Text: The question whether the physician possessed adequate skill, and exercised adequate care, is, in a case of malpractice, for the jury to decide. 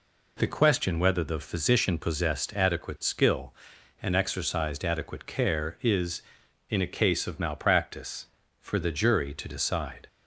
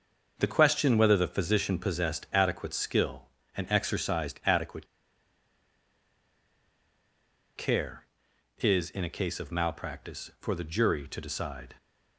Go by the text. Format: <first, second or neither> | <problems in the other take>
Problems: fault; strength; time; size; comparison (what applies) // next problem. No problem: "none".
first | starts louder than the rest; until 1.3 s; 6.5 dB // pauses between "adequate" and "care"; strong; at 4.8 s; 2.7 s long